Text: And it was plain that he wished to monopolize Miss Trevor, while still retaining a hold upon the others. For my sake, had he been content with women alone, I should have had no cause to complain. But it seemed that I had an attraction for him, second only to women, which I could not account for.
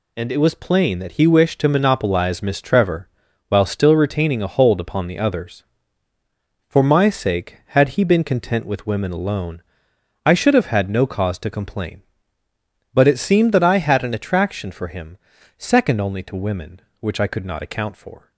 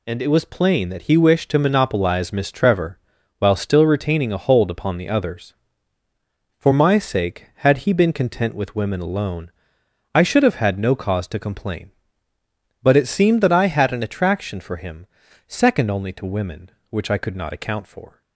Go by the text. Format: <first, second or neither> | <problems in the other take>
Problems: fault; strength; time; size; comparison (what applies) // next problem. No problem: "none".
neither | none